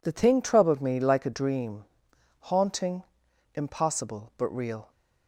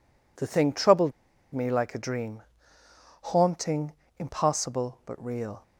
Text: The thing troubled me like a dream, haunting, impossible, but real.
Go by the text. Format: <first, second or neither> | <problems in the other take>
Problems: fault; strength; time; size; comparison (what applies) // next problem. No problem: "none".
first | pauses between "troubled" and "me"; at 1.1 s; 0.42 s long